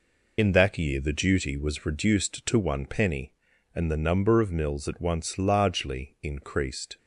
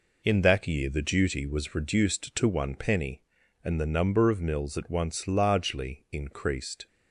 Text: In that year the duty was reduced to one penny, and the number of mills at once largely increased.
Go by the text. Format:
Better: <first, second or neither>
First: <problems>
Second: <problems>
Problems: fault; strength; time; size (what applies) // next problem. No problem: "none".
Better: second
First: loses the start of "In"; at 0.3 s; 30 ms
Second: none